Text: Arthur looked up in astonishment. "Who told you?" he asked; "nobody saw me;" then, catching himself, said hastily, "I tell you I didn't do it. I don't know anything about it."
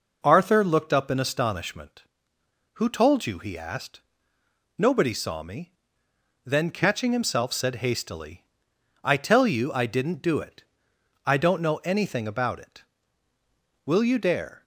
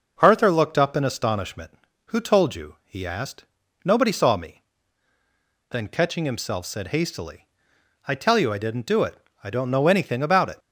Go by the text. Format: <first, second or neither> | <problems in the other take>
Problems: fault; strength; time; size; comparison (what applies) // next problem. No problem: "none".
second | goes on to say "Will you dare"; noticeable; from 13.8 s on; 0.80 s long